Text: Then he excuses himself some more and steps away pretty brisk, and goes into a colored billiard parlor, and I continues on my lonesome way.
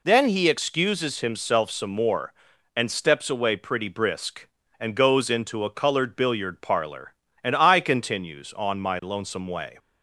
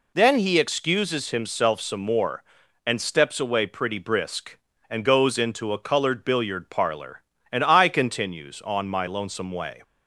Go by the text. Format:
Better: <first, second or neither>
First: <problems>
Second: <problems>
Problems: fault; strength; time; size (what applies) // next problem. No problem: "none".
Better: neither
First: none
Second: none